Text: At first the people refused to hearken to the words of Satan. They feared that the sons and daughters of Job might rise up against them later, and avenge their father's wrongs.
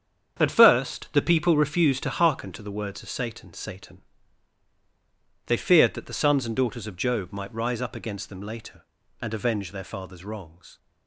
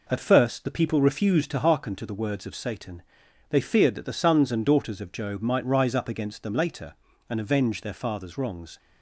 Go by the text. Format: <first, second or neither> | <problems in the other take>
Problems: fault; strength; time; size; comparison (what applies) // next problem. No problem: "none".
second | starts louder than the rest; strong; until 1.4 s; 8 dB // says "Satan" twice; at 3.5 s